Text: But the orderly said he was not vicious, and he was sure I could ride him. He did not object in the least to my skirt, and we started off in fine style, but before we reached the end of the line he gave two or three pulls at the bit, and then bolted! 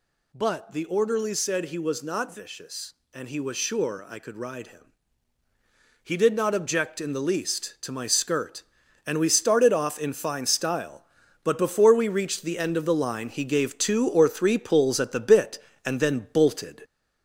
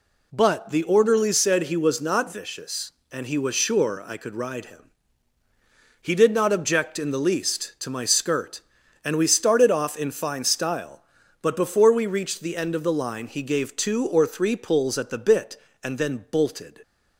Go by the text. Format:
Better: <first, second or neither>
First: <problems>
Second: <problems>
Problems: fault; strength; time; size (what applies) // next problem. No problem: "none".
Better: second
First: gets louder; noticeable; throughout; 5 dB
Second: none